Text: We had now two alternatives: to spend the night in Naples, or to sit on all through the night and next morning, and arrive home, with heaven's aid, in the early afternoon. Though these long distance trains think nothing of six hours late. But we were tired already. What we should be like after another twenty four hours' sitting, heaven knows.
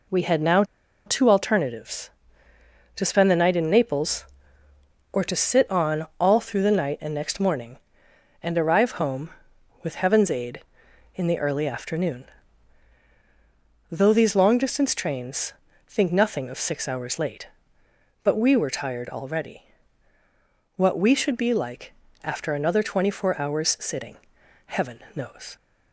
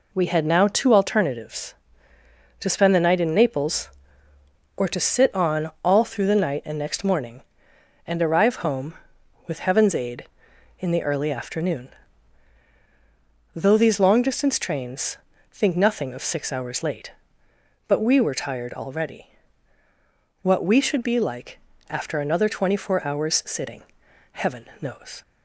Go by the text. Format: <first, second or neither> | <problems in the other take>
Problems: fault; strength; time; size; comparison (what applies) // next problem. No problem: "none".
second | pauses between "now" and "two"; at 0.6 s; 0.42 s long // pauses between "on" and "all"; slight; at 6.0 s; 0.16 s long; slight in the second // pauses between "trains" and "think"; slight; at 15.5 s; 0.34 s long; slight in the second // pauses between "like" and "after"; slight; at 21.9 s; 0.32 s long; slight in the second